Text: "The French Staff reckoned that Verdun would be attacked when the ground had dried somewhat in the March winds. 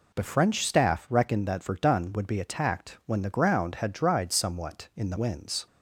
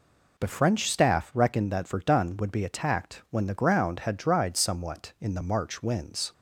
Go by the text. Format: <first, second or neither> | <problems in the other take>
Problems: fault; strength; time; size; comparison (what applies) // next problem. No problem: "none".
second | skips "March"; at 5.1 s